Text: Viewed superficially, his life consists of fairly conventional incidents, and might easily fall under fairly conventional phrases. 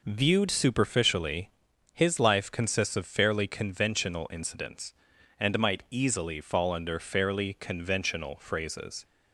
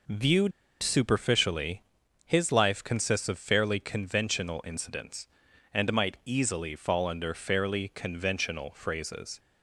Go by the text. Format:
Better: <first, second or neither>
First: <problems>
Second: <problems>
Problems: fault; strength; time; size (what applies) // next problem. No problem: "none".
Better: first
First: none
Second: pauses between "Viewed" and "superficially"; slight; at 0.5 s; 0.31 s long